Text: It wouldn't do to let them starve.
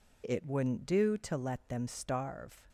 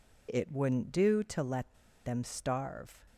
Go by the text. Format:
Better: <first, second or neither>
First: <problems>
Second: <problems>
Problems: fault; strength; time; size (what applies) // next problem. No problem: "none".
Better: first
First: none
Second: pauses between "let" and "them"; slight; at 1.7 s; 0.32 s long